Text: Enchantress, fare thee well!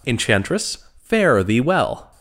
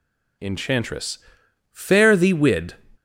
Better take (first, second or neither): first